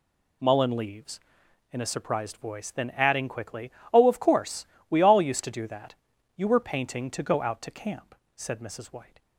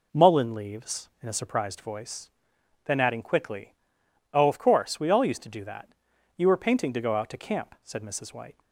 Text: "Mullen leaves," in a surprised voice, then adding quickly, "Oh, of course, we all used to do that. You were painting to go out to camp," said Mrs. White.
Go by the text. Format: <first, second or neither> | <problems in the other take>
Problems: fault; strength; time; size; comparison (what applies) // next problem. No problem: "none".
neither | none